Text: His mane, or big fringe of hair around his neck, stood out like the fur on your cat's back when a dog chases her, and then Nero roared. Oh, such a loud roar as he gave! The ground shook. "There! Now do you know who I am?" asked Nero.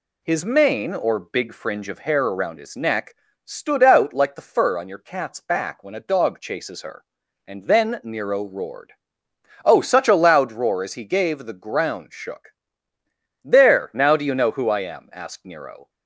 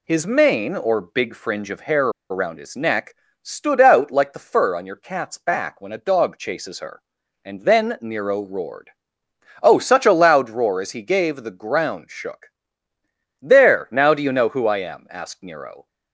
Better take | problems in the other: first | pauses between "hair" and "around"; slight; at 2.0 s; 0.21 s long

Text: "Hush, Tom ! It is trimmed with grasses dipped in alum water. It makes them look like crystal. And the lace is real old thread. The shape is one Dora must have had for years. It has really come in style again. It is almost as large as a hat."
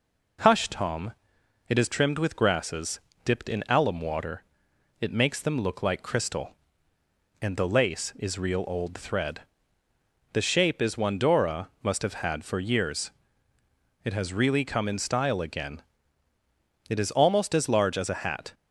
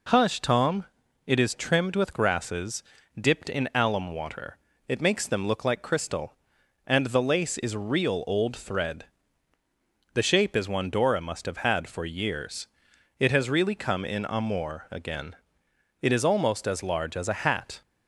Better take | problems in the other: first | pauses between "grasses" and "dipped"; at 2.8 s; 0.38 s long; slight in the first // says "amour" for "style"; at 14.2 s

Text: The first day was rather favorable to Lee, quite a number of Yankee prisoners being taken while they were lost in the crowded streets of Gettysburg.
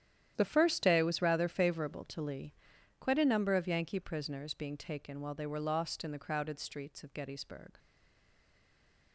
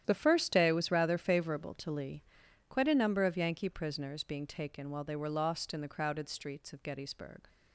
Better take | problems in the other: second | starts louder than the rest; strong; until 1.3 s; 10.5 dB; strong in the second // stays silent after the last word; noticeable; from 7.7 s on; 1.4 s long

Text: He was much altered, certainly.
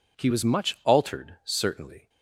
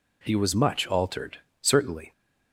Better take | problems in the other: neither | none

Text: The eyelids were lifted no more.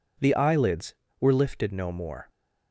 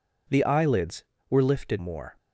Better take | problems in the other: first | skips "no"; at 1.7 s

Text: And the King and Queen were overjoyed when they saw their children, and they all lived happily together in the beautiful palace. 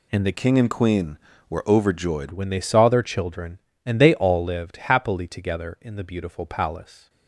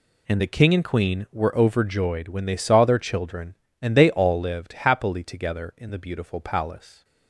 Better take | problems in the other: second | changes voice from "King" to "overjoyed"; from 0.3 to 2.3 s; 2.0 s long

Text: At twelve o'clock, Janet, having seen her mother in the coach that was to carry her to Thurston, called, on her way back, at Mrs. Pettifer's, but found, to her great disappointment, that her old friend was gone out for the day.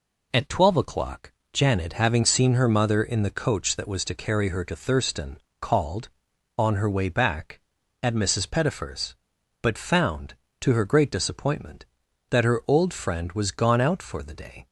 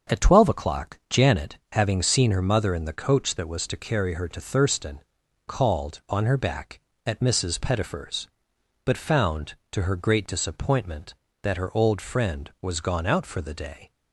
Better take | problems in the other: first | starts louder than the rest; until 1.2 s; 7 dB // skips "way"; at 6.3 s

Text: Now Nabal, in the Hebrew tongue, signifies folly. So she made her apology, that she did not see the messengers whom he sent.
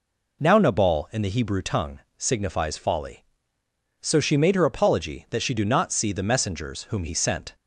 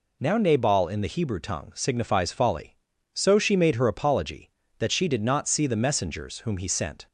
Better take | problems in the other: second | says "do" for "did"; at 5.5 s

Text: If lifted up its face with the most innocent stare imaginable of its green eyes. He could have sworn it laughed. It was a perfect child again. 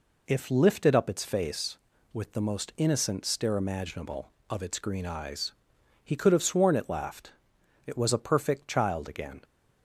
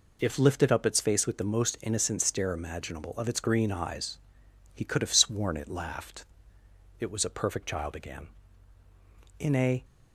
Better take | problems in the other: first | goes on to say "In a"; slight; from 9.3 s on; 0.46 s long

